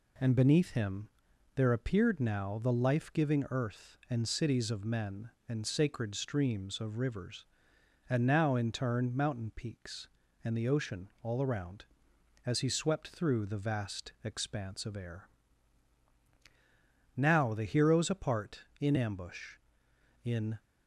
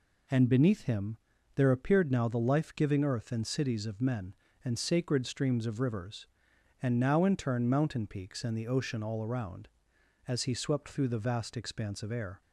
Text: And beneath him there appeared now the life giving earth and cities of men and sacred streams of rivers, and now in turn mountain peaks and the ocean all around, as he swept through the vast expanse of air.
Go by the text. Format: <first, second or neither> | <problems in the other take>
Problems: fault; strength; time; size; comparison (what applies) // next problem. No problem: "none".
second | pauses between "him" and "there"; noticeable; at 1.0 s; 0.46 s long; also in the second // goes on to say "Now the heroes apart in ambush in"; strong; from 17.1 s on; 3.4 s long